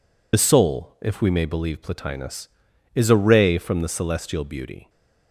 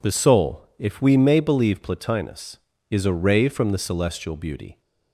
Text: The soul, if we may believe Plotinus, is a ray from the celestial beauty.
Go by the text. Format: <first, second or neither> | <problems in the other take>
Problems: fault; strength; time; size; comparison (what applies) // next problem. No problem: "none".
second | loses the start of "The"; at 0.3 s; 60 ms